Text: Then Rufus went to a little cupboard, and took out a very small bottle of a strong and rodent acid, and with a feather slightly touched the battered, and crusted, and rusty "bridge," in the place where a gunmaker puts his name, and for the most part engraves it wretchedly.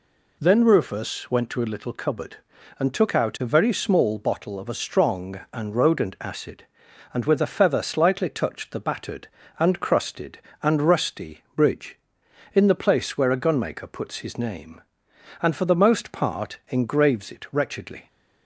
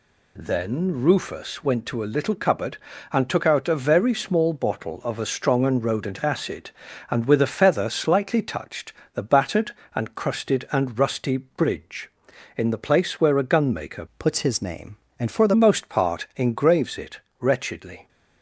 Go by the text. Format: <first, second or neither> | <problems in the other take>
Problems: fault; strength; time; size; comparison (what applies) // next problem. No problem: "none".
first | pauses between "touched" and "the"; slight; at 8.9 s; 0.22 s long // changes voice from "puts" to "the"; from 14.1 to 15.5 s; 1.4 s long // pauses between "it" and "wretchedly"; slight; at 17.1 s; 0.18 s long